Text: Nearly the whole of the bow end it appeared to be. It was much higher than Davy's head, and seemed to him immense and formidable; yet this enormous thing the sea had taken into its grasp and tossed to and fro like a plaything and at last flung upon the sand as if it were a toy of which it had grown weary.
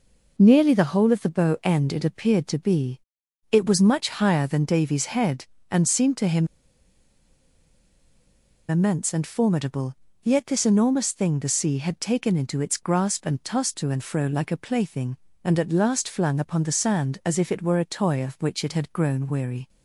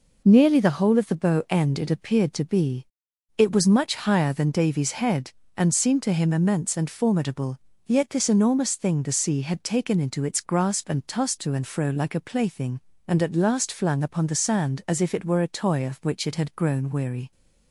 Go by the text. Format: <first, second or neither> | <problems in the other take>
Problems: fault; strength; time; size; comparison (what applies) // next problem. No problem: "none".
second | pauses between "him" and "immense"; strong; at 6.4 s; 2.2 s long